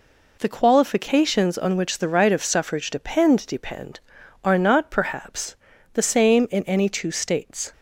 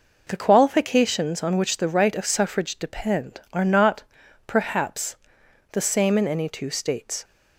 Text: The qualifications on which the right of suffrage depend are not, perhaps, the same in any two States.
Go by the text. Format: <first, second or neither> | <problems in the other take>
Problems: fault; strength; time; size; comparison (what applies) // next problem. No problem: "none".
second | says "depend" twice; at 3.4 s